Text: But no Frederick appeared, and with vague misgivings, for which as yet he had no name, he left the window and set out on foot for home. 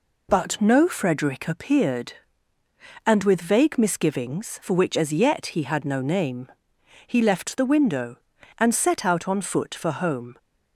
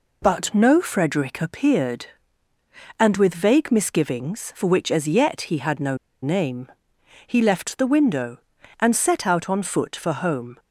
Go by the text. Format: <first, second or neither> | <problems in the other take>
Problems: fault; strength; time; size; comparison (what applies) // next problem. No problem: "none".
first | pauses between "no" and "name"; slight; at 5.9 s; 0.25 s long